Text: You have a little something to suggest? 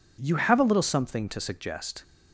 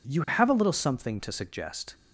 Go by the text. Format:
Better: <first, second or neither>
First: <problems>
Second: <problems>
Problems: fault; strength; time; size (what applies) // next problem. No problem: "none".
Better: neither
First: none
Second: none